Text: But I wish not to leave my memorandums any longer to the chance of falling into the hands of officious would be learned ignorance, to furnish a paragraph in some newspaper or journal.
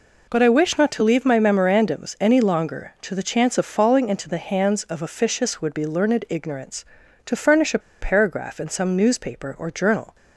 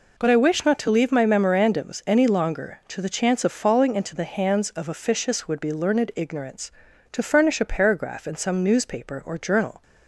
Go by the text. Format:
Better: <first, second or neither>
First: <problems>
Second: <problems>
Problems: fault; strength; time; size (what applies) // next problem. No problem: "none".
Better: second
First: pauses between "a" and "paragraph"; slight; at 7.8 s; 0.21 s long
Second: none